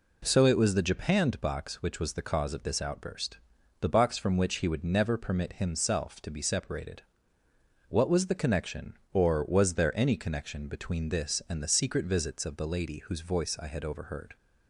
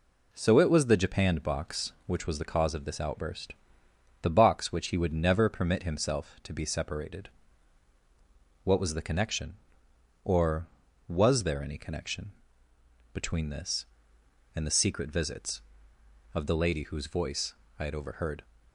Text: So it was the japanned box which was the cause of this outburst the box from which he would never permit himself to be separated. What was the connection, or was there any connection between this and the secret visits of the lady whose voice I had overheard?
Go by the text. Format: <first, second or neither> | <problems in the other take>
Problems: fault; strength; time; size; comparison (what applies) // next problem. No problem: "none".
first | pauses between "outburst" and "the"; noticeable; at 3.5 s; 0.68 s long; also in the first // skips "from"; at 4.7 s // pauses between "connection" and "between"; noticeable; at 12.3 s; 0.82 s long // pauses between "voice" and "I"; slight; at 17.5 s; 0.24 s long